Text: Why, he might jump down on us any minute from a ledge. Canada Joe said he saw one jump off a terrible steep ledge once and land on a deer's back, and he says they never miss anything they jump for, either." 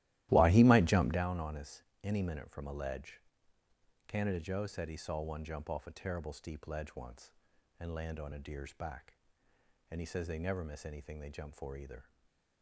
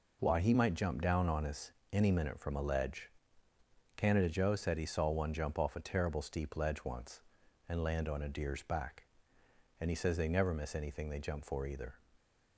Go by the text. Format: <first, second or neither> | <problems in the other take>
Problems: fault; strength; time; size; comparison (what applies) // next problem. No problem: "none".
second | starts louder than the rest; strong; until 1.2 s; 15 dB // pauses between "us" and "any"; slight; at 1.8 s; 0.22 s long; slight in the second // stays silent after the last word; slight; from 12.0 s on; 0.6 s long